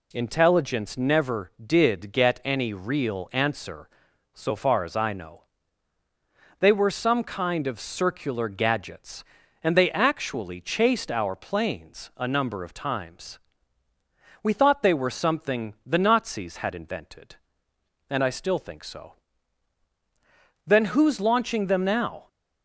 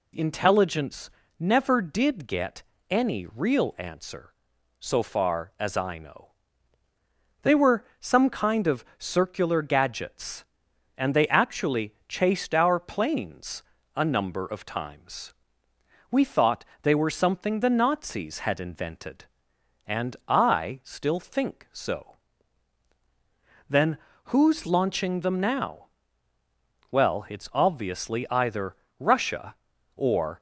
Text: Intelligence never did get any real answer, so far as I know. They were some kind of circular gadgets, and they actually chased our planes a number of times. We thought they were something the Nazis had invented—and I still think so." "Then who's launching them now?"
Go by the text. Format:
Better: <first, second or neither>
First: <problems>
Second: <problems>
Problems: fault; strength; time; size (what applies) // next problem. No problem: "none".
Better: first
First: none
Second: pauses between "Intelligence" and "never"; slight; at 1.0 s; 0.30 s long // pauses between "get" and "any"; slight; at 2.6 s; 0.26 s long // pauses between "were" and "some"; slight; at 7.8 s; 0.16 s long // pauses between "planes" and "a"; slight; at 13.6 s; 0.32 s long // pauses between "thought" and "they"; slight; at 16.6 s; 0.18 s long // pauses between "Then" and "who's"; slight; at 23.9 s; 0.28 s long // goes on to say "Well it's obviously either Russia or"; strong; from 26.9 s on; 3.4 s long